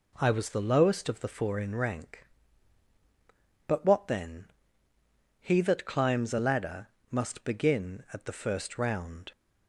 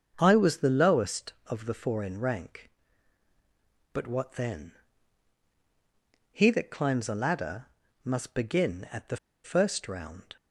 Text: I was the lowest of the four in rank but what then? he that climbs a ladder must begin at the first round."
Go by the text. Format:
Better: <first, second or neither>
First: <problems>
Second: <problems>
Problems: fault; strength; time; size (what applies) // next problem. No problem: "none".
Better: first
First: pauses between "ladder" and "must"; slight; at 6.8 s; 0.24 s long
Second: starts louder than the rest; until 1.1 s; 7 dB // pauses between "ladder" and "must"; at 7.6 s; 0.38 s long // pauses between "the" and "first"; slight; at 9.1 s; 0.27 s long